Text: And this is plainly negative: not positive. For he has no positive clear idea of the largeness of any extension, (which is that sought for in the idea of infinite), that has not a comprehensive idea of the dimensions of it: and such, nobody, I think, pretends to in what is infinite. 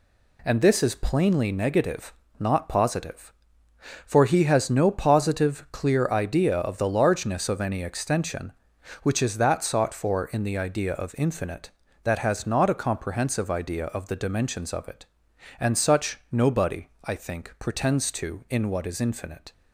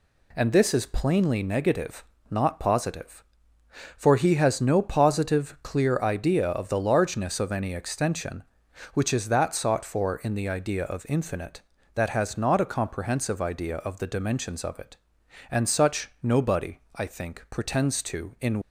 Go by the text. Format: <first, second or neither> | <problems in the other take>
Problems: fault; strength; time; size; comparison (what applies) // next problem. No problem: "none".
first | stops before "what is infinite"; at 18.6 s